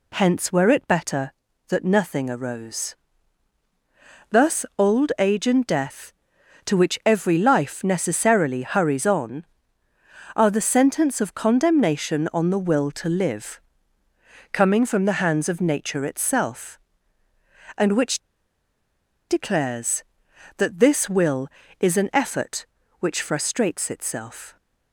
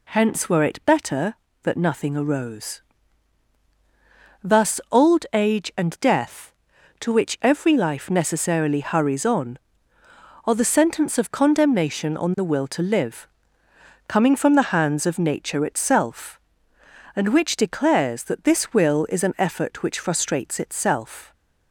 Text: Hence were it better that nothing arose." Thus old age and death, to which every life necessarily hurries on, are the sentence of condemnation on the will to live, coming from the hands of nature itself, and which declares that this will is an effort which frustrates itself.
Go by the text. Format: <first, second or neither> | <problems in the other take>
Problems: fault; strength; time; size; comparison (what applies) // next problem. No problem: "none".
second | pauses between "which" and "declares"; at 18.1 s; 1.1 s long